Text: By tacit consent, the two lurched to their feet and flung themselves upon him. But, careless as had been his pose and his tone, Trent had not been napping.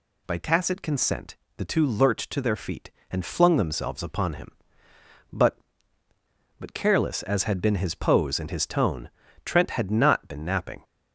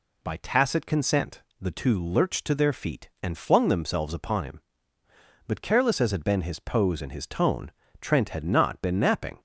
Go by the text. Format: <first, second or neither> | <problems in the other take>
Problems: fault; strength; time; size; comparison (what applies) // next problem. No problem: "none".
second | says "But" twice; at 6.5 s